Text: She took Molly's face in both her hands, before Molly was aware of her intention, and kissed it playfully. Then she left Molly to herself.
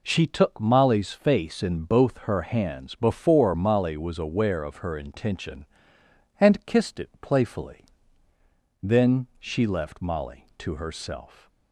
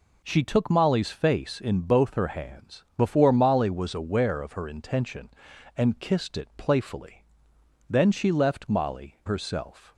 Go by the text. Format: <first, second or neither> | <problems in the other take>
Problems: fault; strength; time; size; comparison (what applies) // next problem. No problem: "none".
first | skips "to"; at 9.2 s